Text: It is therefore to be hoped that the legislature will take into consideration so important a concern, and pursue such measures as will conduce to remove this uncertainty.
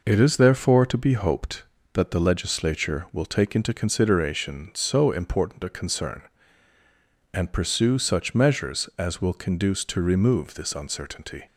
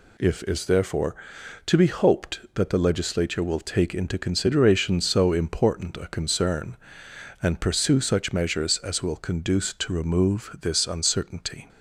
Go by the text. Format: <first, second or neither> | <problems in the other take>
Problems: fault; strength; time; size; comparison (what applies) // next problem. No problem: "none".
first | says "If" for "It"; at 0.1 s